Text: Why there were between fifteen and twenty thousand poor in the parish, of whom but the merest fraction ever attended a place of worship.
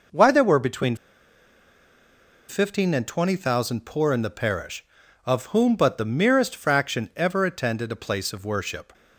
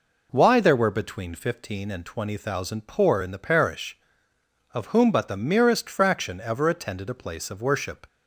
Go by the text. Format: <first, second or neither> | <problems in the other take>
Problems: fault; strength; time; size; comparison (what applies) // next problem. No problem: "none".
second | pauses between "between" and "fifteen"; strong; at 0.9 s; 1.5 s long